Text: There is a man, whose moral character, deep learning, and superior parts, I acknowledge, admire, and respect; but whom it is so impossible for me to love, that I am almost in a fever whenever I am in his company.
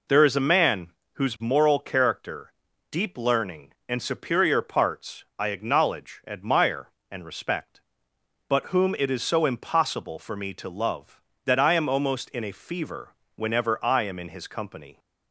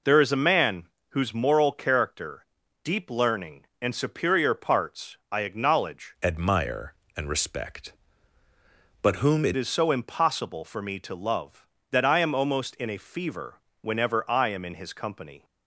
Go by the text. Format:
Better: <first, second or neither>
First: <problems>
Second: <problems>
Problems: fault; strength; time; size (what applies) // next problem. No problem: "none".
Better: first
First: pauses between "fever" and "whenever"; slight; at 13.1 s; 0.22 s long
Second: changes voice from "admire" to "it"; from 6.2 to 9.5 s; 3.3 s long // pauses between "fever" and "whenever"; slight; at 13.6 s; 0.22 s long